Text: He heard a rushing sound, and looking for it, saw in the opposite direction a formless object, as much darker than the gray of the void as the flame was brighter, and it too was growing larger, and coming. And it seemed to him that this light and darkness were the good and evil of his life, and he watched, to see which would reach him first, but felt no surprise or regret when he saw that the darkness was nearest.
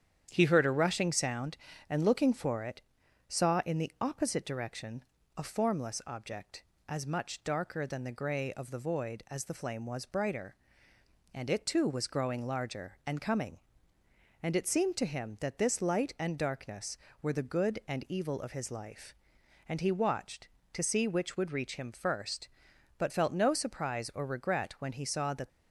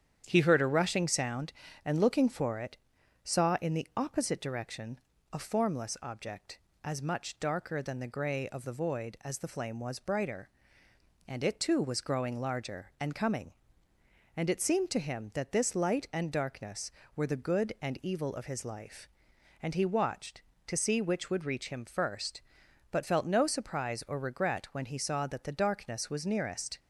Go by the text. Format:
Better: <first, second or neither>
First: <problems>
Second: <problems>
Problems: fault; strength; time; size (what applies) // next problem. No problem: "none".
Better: second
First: starts louder than the rest; strong; until 1.3 s; 9 dB // pauses between "direction" and "a"; slight; at 5.0 s; 0.34 s long // stops before "the darkness was nearest"; at 25.4 s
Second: starts louder than the rest; strong; until 1.2 s; 9 dB // pauses between "direction" and "a"; slight; at 4.9 s; 0.34 s long